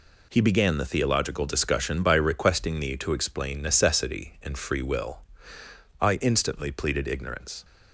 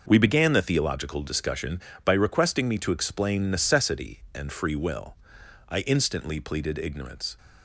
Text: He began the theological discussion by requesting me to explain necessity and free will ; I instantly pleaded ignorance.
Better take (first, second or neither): first